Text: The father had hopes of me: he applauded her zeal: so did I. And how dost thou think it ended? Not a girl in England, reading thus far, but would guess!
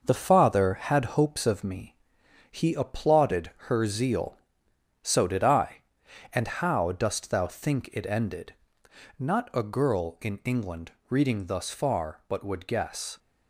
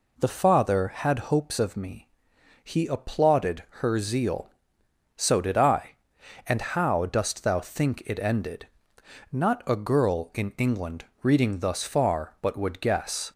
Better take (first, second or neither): second